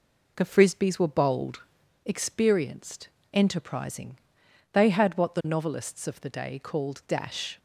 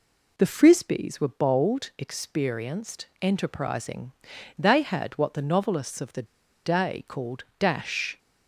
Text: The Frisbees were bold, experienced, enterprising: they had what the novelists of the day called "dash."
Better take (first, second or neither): first